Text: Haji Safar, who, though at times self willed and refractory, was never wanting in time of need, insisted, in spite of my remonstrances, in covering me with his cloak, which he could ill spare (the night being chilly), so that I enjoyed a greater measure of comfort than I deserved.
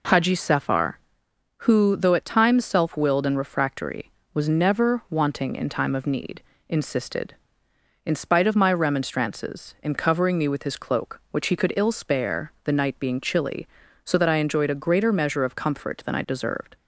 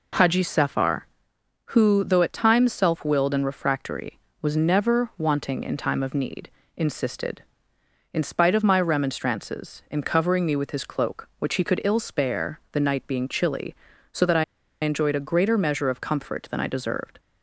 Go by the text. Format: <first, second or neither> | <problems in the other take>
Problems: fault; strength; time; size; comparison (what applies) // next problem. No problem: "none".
first | pauses between "I" and "enjoyed"; at 14.4 s; 0.37 s long